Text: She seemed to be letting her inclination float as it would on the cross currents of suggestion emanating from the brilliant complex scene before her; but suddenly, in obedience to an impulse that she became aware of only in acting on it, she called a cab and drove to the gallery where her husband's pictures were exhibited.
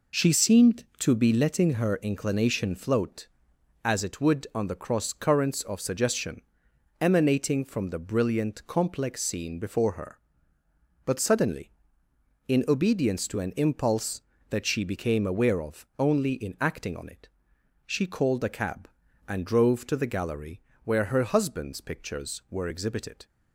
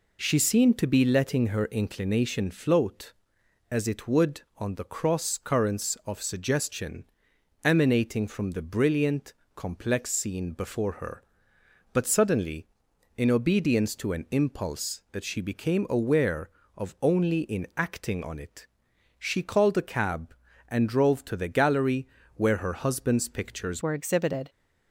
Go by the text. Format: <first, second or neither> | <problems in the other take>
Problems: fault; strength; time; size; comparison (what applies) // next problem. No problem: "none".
first | pauses between "suggestion" and "emanating"; noticeable; at 7.0 s; 0.58 s long; noticeable in the first // pauses between "brilliant" and "complex"; slight; at 9.3 s; 0.24 s long // pauses between "gallery" and "where"; slight; at 22.0 s; 0.28 s long; slight in the first // changes voice at "were"; from 23.8 s on; 0.6 s long